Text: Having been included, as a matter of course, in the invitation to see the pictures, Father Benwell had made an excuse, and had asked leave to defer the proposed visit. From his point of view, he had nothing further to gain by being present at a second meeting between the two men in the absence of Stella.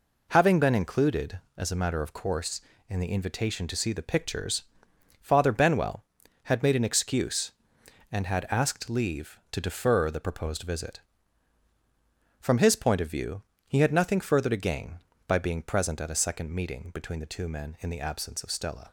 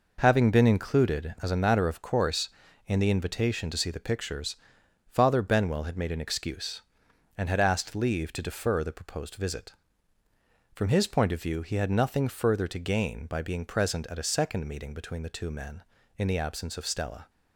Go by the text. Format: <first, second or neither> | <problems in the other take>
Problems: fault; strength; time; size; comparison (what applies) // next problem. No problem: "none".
neither | none